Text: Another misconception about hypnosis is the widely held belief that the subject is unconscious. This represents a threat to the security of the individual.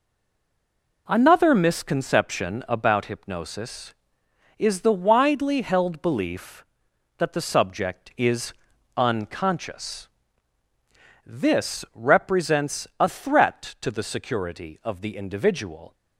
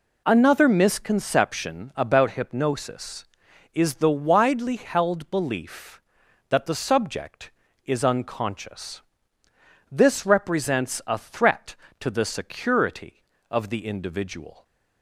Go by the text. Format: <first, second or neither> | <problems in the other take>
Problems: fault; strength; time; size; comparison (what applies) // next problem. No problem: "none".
second | stays silent before the first word; until 1.0 s; 1.0 s long // pauses between "is" and "unconscious"; at 8.5 s; 0.44 s long